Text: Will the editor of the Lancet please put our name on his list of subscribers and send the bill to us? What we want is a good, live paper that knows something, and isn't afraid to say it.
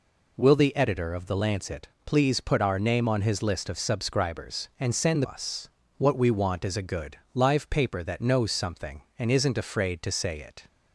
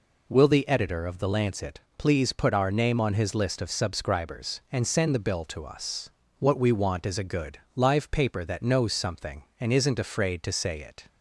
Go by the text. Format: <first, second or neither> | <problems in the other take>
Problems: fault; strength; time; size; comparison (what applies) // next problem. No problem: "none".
second | pauses between "Lancet" and "please"; slight; at 1.8 s; 0.16 s long; slight in the second // skips "the bill to"; at 5.2 s